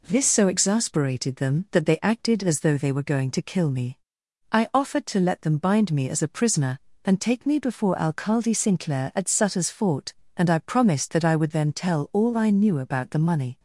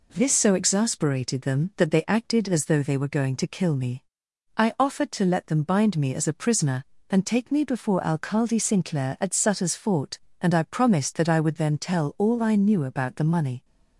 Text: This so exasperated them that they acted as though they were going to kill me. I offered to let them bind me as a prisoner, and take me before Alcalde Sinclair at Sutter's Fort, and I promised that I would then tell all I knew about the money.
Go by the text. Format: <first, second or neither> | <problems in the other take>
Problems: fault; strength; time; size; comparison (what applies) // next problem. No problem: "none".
neither | none